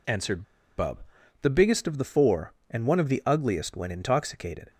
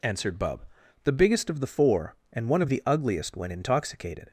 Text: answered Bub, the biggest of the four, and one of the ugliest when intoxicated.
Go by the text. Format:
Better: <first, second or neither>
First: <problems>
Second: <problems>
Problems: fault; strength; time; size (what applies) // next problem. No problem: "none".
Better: second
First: pauses between "answered" and "Bub"; slight; at 0.4 s; 0.35 s long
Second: none